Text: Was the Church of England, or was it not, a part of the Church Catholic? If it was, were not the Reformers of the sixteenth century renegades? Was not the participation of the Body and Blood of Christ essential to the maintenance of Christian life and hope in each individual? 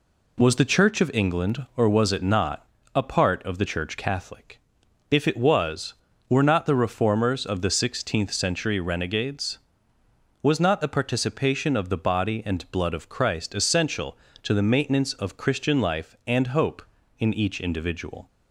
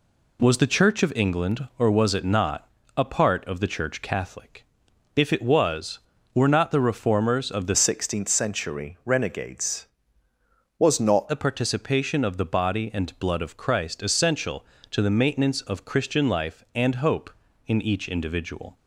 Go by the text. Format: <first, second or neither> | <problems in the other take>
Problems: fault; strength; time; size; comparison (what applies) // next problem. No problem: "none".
first | changes voice from "sixteenth" to "not"; from 7.7 to 11.2 s; 3.5 s long